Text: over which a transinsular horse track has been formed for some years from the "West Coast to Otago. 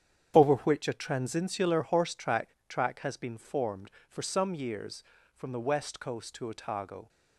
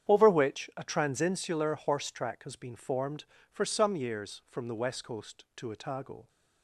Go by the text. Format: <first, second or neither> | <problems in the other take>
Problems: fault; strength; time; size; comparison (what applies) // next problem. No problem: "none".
second | starts louder than the rest; strong; until 1.3 s; 9 dB; strong in the second // says "track" twice; at 2.6 s